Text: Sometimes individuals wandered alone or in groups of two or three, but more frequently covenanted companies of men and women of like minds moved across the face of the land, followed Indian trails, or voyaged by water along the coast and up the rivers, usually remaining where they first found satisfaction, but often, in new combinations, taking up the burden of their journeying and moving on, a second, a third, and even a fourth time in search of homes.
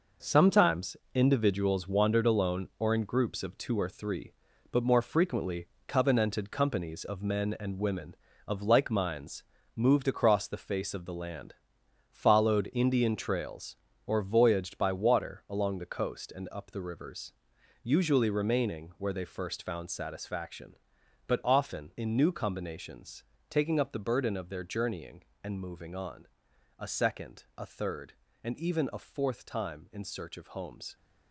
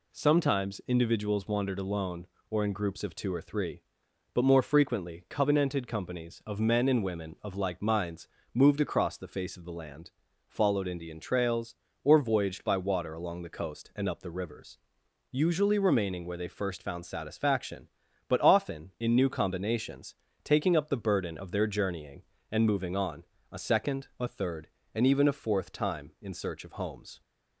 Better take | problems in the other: second | gets quieter; strong; throughout; 8.5 dB // pauses between "Sometimes" and "individuals"; slight; at 0.9 s; 0.20 s long // pauses between "frequently" and "covenanted"; slight; at 5.6 s; 0.22 s long // pauses between "minds" and "moved"; slight; at 9.4 s; 0.34 s long; slight in the second

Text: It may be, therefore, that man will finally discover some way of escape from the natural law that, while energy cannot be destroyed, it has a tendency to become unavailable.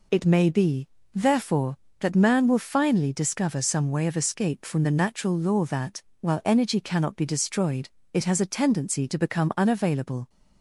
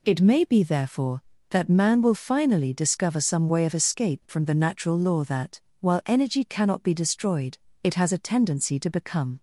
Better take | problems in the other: first | stops before "unavailable"; at 9.3 s

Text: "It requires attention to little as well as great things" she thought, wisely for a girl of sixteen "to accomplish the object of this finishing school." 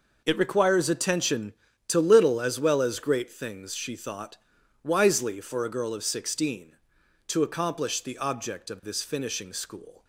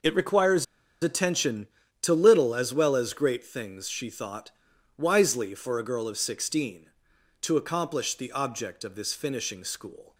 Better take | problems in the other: first | pauses between "requires" and "attention"; at 0.6 s; 0.37 s long

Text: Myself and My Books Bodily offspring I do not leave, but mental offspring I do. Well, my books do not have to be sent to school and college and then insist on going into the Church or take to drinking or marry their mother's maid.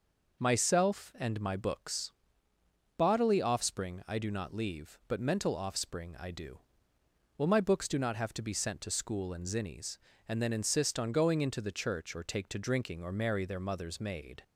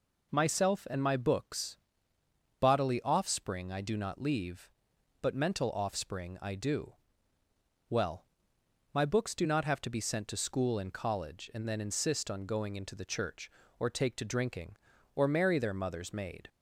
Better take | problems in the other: second | pauses between "Books" and "Bodily"; noticeable; at 2.1 s; 0.88 s long; noticeable in the second // says "zinnies" for "college"; at 9.4 s

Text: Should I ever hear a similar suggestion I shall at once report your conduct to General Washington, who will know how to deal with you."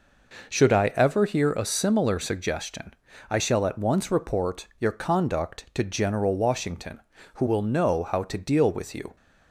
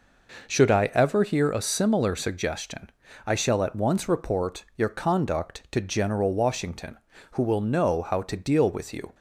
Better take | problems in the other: neither | pauses between "suggestion" and "I"; slight; the same in both

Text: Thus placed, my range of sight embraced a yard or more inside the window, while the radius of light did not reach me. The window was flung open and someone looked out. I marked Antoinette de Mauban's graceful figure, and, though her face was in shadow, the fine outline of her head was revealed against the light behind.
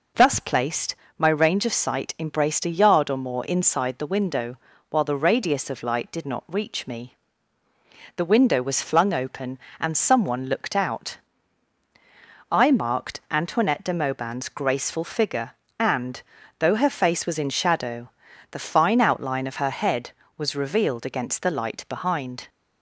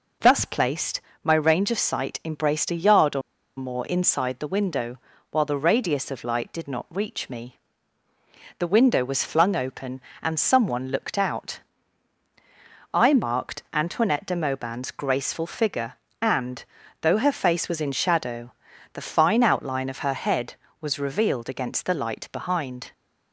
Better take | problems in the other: first | pauses between "or" and "more"; at 3.2 s; 0.36 s long

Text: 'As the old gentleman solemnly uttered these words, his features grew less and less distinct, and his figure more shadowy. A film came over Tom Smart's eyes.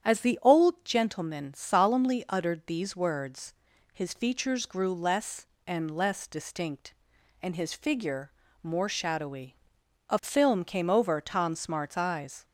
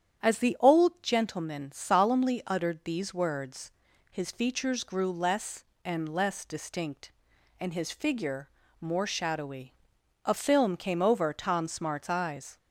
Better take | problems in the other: neither | starts louder than the rest; strong; the same in both // pauses between "figure" and "more"; slight; the same in both

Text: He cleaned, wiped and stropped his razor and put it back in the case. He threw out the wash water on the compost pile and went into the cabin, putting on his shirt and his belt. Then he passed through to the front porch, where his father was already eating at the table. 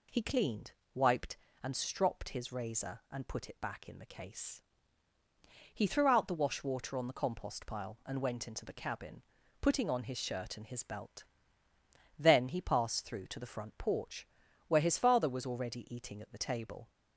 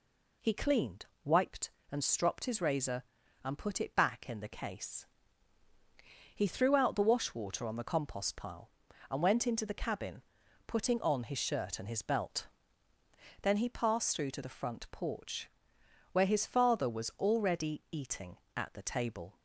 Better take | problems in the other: neither | none

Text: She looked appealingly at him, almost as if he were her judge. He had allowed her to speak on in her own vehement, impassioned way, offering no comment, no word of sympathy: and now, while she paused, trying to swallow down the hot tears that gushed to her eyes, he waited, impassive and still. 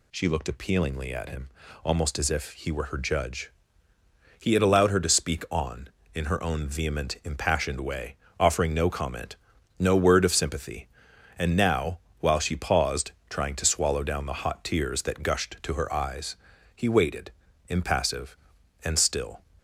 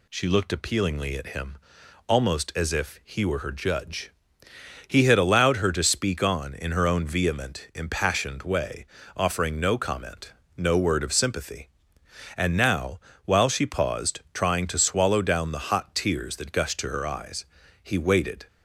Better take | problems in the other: first | stops before "impassive and still"; at 18.4 s

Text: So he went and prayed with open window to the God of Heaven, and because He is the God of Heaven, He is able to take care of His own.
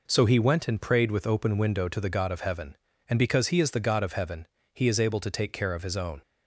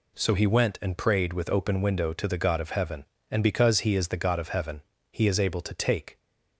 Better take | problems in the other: first | stops before "care of His own"; at 6.1 s

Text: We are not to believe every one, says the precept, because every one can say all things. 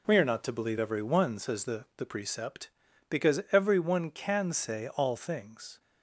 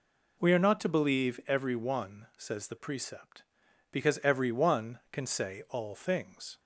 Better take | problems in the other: second | says "the" twice; at 1.9 s

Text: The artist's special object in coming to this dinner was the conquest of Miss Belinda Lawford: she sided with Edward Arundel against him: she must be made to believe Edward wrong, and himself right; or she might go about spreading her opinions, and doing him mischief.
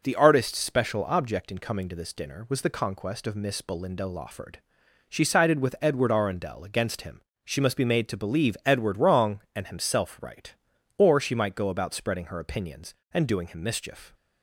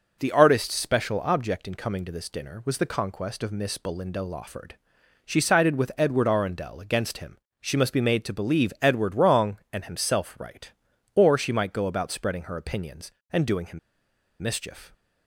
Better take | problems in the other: first | pauses between "him" and "mischief"; noticeable; at 13.7 s; 0.61 s long

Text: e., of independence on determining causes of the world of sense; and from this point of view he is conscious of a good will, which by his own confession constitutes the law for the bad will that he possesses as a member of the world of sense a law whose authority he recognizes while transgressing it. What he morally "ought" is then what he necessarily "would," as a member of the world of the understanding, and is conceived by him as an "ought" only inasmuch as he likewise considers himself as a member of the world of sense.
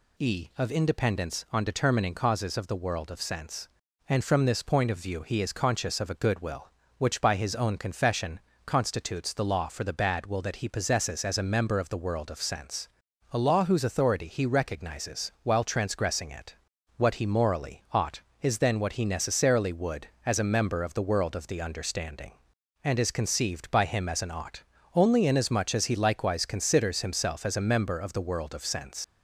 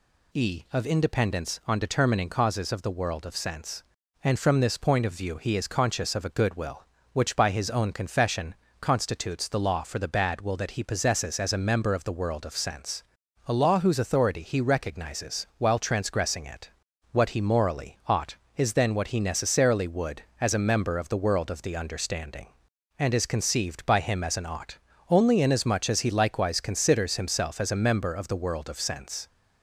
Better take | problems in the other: second | pauses between "confession" and "constitutes"; slight; at 8.3 s; 0.26 s long; slight in the second // pauses between "sense" and "a"; at 12.8 s; 0.44 s long; also in the second // pauses between "ought" and "only"; slight; at 24.6 s; 0.32 s long; slight in the second // leaves "sense" unfinished; at 29.0 s; 85 ms

